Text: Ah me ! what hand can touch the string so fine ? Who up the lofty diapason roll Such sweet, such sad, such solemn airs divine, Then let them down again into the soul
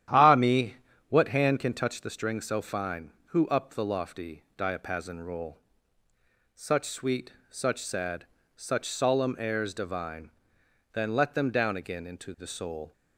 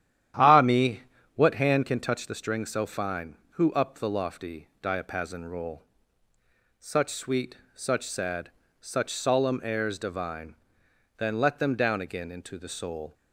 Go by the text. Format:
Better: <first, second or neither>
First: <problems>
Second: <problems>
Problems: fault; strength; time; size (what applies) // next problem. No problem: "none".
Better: neither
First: starts louder than the rest; strong; until 1.4 s; 11 dB // pauses between "roll" and "Such"; noticeable; at 5.5 s; 0.96 s long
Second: starts louder than the rest; strong; until 1.7 s; 11 dB // pauses between "roll" and "Such"; noticeable; at 5.8 s; 0.96 s long